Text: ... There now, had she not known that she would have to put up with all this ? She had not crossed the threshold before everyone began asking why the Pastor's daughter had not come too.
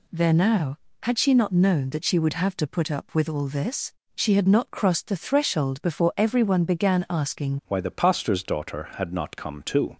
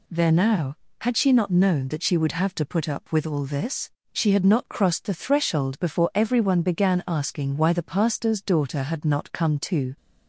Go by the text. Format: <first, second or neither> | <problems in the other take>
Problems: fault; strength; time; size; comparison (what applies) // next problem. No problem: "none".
second | changes voice at "why"; from 7.6 s on; 2.3 s long